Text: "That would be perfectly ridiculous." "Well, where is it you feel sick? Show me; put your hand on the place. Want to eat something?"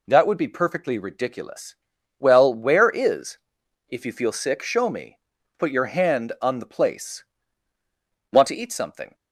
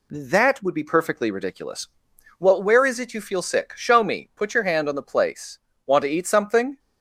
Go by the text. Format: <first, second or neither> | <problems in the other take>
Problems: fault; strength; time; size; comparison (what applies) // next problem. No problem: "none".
second | says "if" for "it"; at 3.8 s